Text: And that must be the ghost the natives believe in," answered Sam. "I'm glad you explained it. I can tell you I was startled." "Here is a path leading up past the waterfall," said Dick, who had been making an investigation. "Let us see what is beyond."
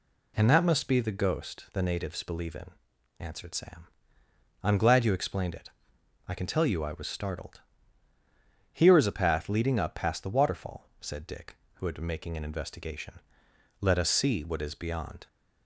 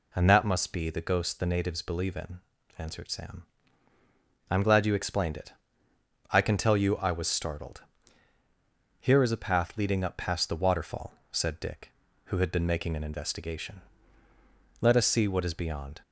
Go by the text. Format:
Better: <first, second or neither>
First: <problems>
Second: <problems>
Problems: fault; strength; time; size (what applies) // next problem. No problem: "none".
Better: neither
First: none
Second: none